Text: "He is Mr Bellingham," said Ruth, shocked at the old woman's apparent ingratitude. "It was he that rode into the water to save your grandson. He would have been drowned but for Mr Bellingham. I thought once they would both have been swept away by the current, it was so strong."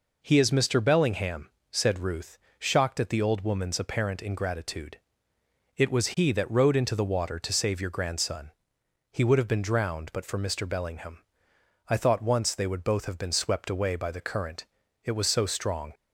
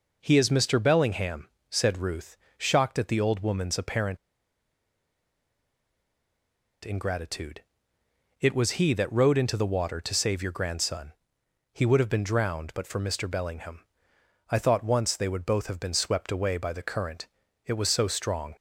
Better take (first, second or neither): first